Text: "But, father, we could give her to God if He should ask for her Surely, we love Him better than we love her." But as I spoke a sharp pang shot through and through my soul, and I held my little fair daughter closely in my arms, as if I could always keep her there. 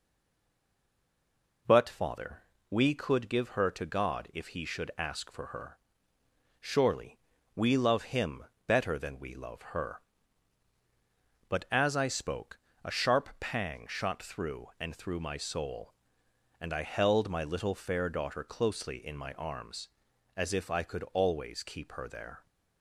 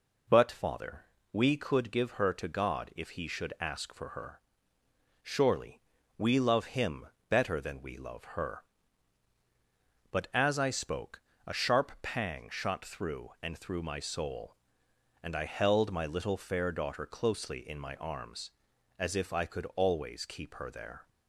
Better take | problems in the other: second | stays silent before the first word; noticeable; until 1.6 s; 1.6 s long // pauses between "her" and "Surely"; noticeable; at 5.7 s; 0.82 s long; noticeable in the second // pauses between "Him" and "better"; slight; at 8.4 s; 0.22 s long; slight in the second // pauses between "spoke" and "a"; slight; at 12.5 s; 0.26 s long; slight in the second

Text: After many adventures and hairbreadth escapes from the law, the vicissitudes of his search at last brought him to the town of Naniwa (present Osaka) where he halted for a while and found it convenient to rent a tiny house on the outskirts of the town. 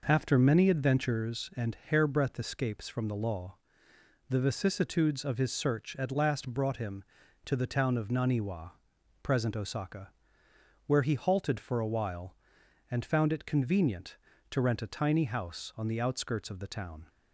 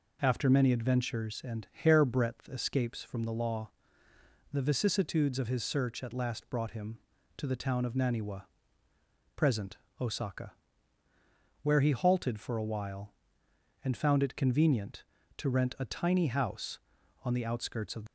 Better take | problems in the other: first | pauses between "present" and "Osaka"; slight; at 9.7 s; 0.20 s long // stops before "the town"; at 18.0 s

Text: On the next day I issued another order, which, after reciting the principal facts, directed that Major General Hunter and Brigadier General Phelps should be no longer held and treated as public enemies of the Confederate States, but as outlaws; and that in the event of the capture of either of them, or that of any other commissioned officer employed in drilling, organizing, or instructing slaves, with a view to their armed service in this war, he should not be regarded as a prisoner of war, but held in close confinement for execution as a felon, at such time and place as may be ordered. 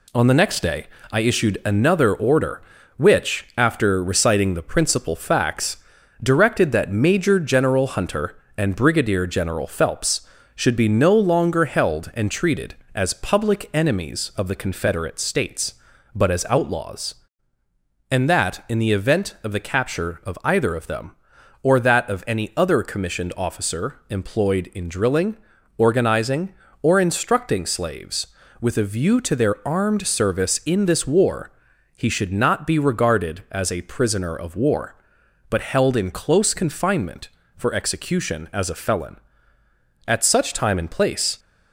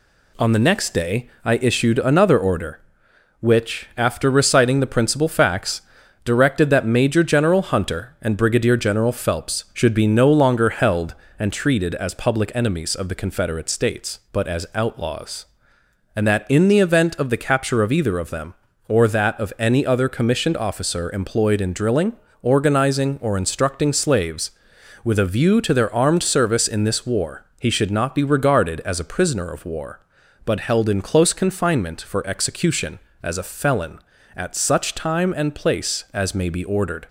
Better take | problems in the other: second | pauses between "day" and "I"; slight; at 0.8 s; 0.24 s long // stops before "as may be ordered"; at 41.3 s

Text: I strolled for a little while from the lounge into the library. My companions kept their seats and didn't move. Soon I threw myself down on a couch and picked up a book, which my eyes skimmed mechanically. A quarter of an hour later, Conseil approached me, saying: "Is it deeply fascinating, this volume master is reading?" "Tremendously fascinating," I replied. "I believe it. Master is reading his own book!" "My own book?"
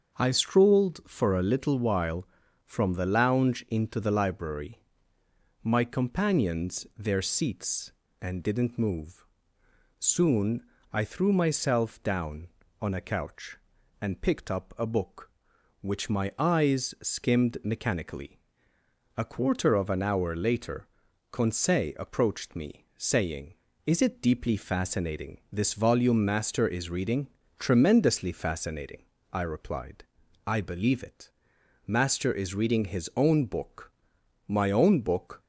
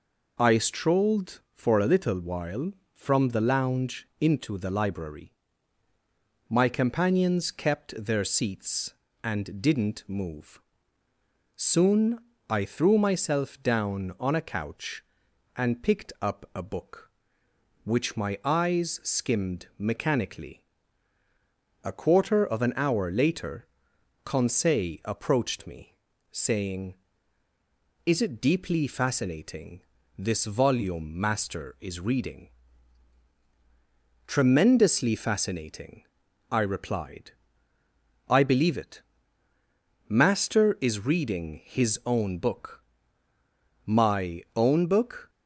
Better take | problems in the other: second | starts louder than the rest; until 1.2 s; 7 dB // skips "kept"; at 6.9 s // pauses between "Soon" and "I"; slight; at 10.6 s; 0.30 s long; slight in the second

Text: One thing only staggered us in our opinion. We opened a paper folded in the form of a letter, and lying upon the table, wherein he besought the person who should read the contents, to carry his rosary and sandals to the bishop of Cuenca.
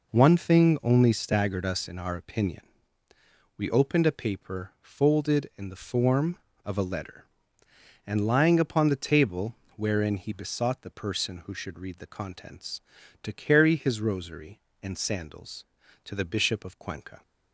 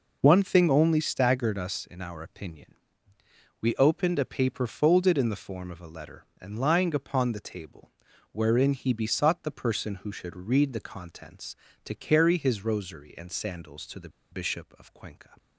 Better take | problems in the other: first | pauses between "the" and "bishop"; slight; at 14.1 s; 0.21 s long

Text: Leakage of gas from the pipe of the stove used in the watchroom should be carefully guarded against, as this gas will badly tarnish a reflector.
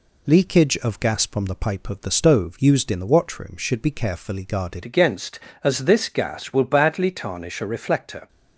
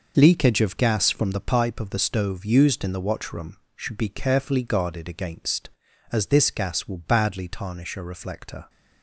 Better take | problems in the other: second | changes voice at "against"; from 4.8 s on; 3.4 s long

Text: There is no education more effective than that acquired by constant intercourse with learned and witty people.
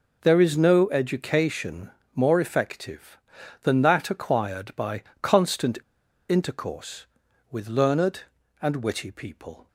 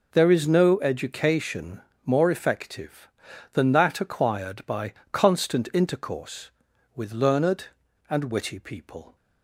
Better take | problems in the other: second | pauses between "education" and "more"; slight; at 1.9 s; 0.22 s long; slight in the second // pauses between "by" and "constant"; slight; at 5.0 s; 0.18 s long; slight in the second // pauses between "constant" and "intercourse"; noticeable; at 5.7 s; 0.49 s long

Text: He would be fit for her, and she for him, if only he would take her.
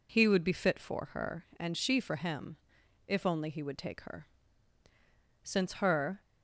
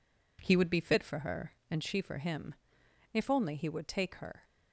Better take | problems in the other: second | goes on to say "Since her"; noticeable; from 5.4 s on; 0.76 s long

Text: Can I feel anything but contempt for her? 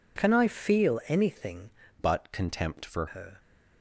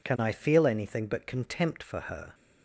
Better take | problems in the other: second | changes voice from "but" to "for"; from 1.9 to 3.0 s; 1.1 s long

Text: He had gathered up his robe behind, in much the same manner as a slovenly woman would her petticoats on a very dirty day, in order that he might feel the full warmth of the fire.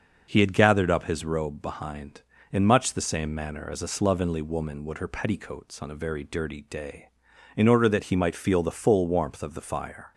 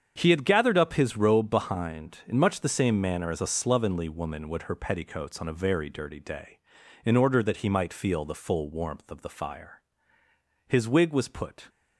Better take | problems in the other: first | starts louder than the rest; strong; until 1.1 s; 7.5 dB; noticeable in the first // goes on to say "His wig was put"; noticeable; from 10.6 s on; 1.0 s long

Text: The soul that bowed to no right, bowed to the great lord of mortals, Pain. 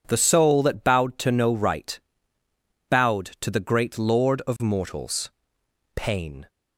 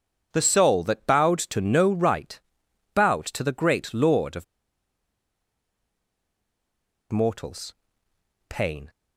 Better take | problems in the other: first | pauses between "of" and "mortals"; strong; at 4.4 s; 2.6 s long

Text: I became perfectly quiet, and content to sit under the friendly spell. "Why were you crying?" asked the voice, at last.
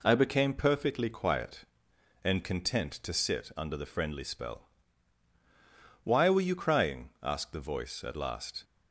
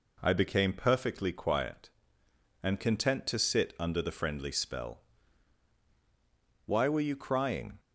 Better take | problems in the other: first | stops before "asked the voice at last"; at 7.7 s

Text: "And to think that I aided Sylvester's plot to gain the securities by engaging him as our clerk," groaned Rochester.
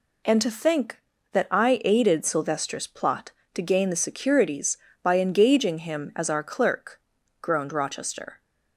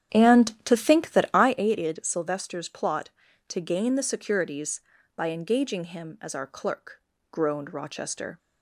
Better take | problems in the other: first | starts louder than the rest; strong; until 1.7 s; 10 dB

